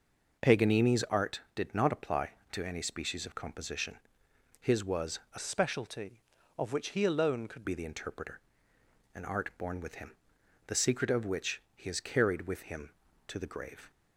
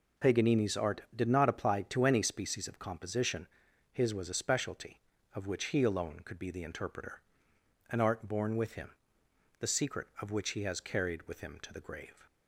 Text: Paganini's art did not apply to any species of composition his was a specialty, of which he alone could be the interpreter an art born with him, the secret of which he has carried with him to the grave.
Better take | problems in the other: second | pauses between "composition" and "his"; noticeable; at 3.9 s; 0.62 s long; noticeable in the second // pauses between "was" and "a"; slight; at 5.1 s; 0.16 s long // changes voice from "specialty" to "could"; from 5.3 to 7.6 s; 2.3 s long // pauses between "interpreter" and "an"; noticeable; at 8.3 s; 0.76 s long; noticeable in the second

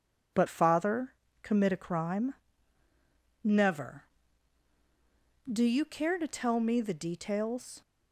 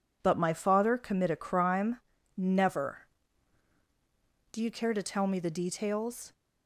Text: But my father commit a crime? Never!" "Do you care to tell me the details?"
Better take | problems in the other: second | skips "my"; at 0.4 s // pauses between "father" and "commit"; slight; at 1.1 s; 0.30 s long

